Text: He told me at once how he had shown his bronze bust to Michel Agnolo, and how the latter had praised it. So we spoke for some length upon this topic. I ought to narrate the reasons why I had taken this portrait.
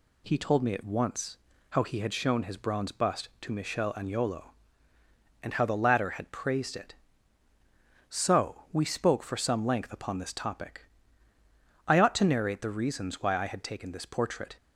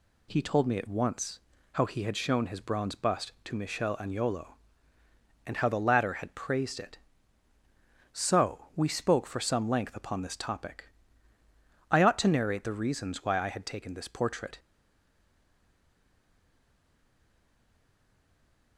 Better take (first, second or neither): first